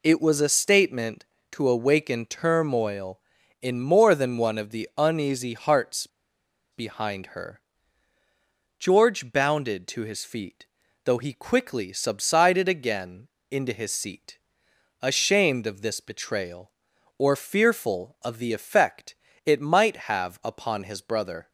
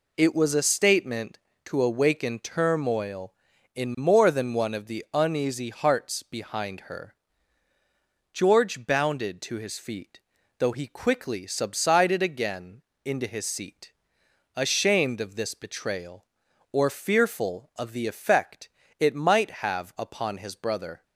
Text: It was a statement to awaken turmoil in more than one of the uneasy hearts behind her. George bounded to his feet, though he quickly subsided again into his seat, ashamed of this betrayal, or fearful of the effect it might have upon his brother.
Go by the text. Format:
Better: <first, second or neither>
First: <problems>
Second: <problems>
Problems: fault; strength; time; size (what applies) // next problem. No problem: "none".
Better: second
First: pauses between "hearts" and "behind"; noticeable; at 6.0 s; 0.65 s long // pauses between "again" and "into"; slight; at 13.2 s; 0.22 s long // pauses between "effect" and "it"; slight; at 19.1 s; 0.30 s long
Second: pauses between "again" and "into"; slight; at 12.8 s; 0.22 s long // pauses between "effect" and "it"; slight; at 18.6 s; 0.30 s long